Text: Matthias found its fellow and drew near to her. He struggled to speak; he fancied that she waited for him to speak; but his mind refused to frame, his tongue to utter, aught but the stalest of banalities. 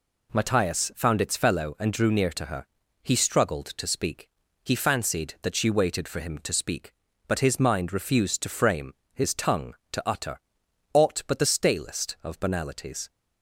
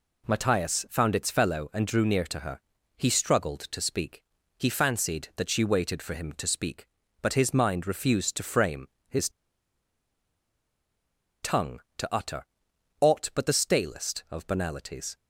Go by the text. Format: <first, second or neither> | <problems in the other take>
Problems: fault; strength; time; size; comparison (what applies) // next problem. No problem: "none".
first | pauses between "his" and "tongue"; strong; at 9.2 s; 2.1 s long